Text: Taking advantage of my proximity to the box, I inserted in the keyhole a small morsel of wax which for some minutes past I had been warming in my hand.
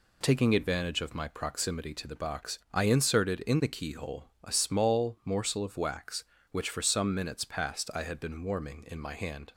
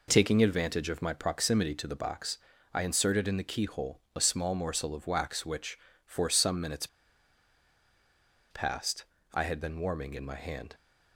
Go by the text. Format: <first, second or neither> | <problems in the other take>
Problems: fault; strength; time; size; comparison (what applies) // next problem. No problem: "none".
first | pauses between "keyhole" and "a"; slight; at 3.9 s; 0.16 s long; slight in the first // pauses between "minutes" and "past"; strong; at 6.8 s; 1.6 s long // pauses between "past" and "I"; slight; at 9.0 s; 0.28 s long